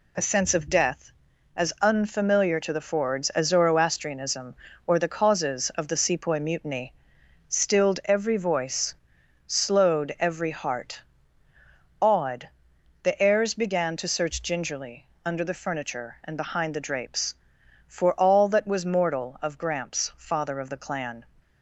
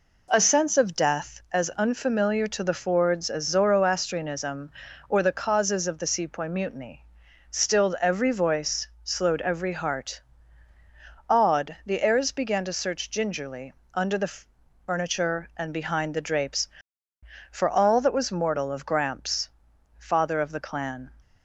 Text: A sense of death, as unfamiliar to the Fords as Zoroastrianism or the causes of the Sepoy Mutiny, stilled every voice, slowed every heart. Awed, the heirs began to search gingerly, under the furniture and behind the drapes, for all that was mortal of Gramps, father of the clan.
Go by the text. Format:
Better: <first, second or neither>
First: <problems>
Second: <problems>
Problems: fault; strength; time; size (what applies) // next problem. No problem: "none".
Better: first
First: none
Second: starts louder than the rest; until 1.5 s; 4 dB // pauses between "the" and "furniture"; noticeable; at 14.3 s; 0.54 s long